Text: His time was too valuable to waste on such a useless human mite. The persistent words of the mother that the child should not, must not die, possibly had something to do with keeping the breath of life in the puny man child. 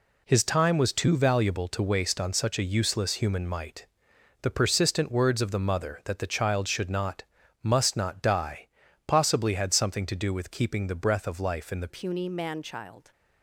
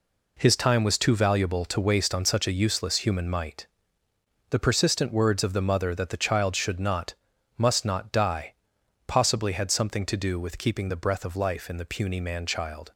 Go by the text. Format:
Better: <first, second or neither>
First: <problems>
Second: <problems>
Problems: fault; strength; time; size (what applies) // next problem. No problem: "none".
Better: second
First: changes voice at "puny"; from 11.8 s on; 1.3 s long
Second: none